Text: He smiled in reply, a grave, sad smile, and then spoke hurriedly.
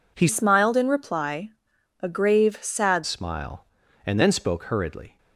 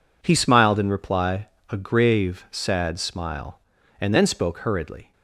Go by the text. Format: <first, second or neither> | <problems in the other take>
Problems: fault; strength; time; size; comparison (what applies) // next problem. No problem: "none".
second | changes voice from "smiled" to "sad"; from 0.2 to 3.0 s; 2.8 s long